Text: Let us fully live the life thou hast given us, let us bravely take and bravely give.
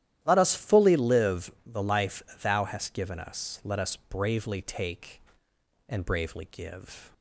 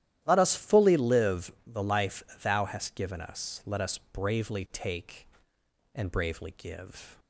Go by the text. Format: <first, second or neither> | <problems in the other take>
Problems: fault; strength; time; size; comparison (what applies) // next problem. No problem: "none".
neither | starts louder than the rest; strong; the same in both // pauses between "live" and "the"; slight; the same in both // pauses between "life" and "thou"; slight; the same in both